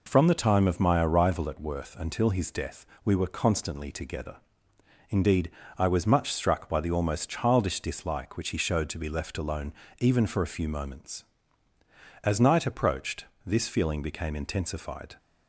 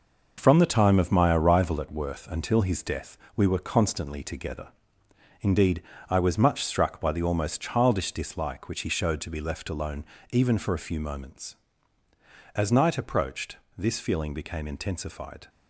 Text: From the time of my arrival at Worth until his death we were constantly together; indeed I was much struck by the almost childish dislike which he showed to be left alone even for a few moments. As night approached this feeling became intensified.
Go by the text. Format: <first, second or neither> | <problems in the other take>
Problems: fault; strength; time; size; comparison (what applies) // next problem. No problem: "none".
first | gets quieter; strong; throughout; 7.5 dB // pauses between "death" and "we"; slight; at 3.1 s; 0.18 s long; slight in the first // pauses between "indeed" and "I"; slight; at 5.8 s; 0.26 s long; slight in the first // pauses between "alone" and "even"; slight; at 10.0 s; 0.26 s long; slight in the first // pauses between "approached" and "this"; slight; at 13.5 s; 0.20 s long; slight in the first